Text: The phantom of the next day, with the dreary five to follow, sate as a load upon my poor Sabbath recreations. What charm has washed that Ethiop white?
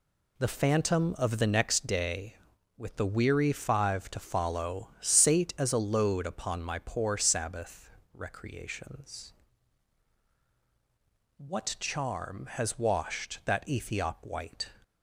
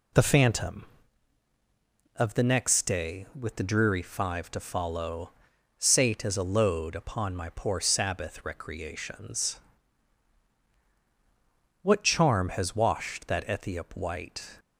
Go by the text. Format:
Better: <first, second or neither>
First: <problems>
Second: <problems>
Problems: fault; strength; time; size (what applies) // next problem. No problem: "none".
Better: second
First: says "weary" for "dreary"; at 3.0 s // pauses between "Sabbath" and "recreations"; slight; at 7.8 s; 0.22 s long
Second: none